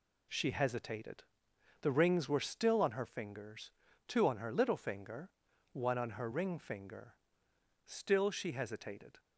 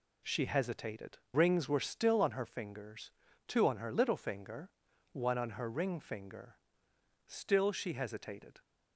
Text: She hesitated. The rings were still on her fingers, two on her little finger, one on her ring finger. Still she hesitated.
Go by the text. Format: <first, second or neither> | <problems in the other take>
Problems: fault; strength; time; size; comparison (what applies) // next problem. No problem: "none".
first | skips "The"; at 1.2 s